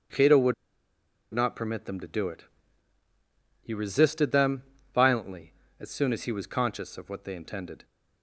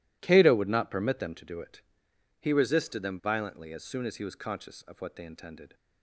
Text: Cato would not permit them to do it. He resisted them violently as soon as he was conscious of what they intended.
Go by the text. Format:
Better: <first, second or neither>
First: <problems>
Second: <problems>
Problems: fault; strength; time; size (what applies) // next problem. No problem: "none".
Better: second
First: starts louder than the rest; strong; until 1.9 s; 8 dB // pauses between "would" and "not"; noticeable; at 0.5 s; 0.80 s long // pauses between "them" and "violently"; slight; at 4.6 s; 0.32 s long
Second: none